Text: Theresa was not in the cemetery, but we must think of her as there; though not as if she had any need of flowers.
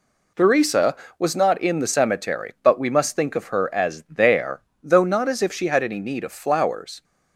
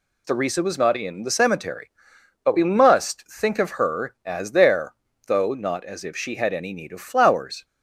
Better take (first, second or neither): neither